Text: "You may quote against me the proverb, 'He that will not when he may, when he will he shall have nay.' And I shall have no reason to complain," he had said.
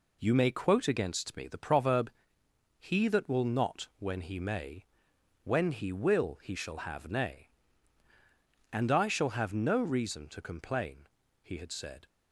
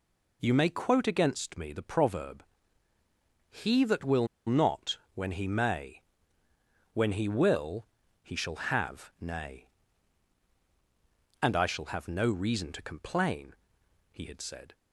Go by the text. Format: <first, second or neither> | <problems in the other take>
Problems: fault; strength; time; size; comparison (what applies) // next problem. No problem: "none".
first | pauses between "will" and "not"; slight; at 4.2 s; 0.20 s long // pauses between "not" and "when"; slight; at 4.9 s; 0.16 s long // pauses between "will" and "he"; slight; at 7.8 s; 0.36 s long